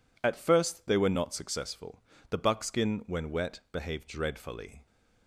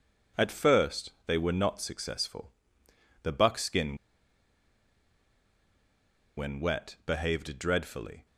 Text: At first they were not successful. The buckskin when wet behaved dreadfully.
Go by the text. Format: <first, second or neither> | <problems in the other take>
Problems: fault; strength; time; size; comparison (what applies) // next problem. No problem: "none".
first | pauses between "first" and "they"; slight; at 1.1 s; 0.16 s long // pauses between "buckskin" and "when"; strong; at 3.9 s; 2.4 s long